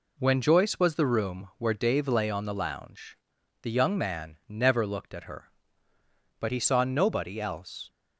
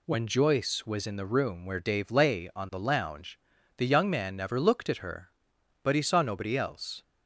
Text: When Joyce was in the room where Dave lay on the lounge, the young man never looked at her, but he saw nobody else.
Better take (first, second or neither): second